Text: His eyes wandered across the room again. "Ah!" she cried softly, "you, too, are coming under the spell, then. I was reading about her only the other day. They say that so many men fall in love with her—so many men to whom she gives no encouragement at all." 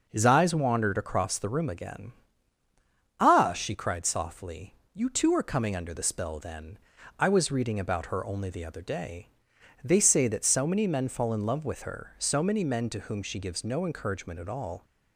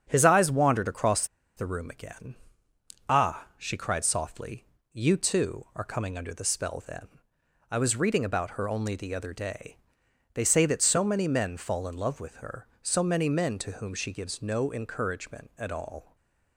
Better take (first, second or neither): first